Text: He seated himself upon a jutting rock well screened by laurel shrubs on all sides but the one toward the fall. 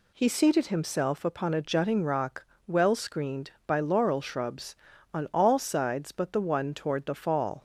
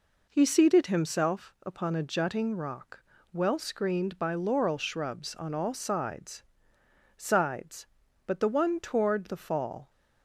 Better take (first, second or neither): first